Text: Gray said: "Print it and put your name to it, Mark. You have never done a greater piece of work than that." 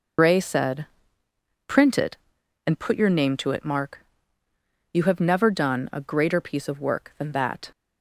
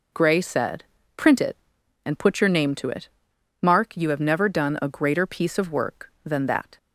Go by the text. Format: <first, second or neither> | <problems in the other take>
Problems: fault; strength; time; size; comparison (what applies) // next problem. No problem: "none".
second | loses the start of "Gray"; at 0.1 s; 75 ms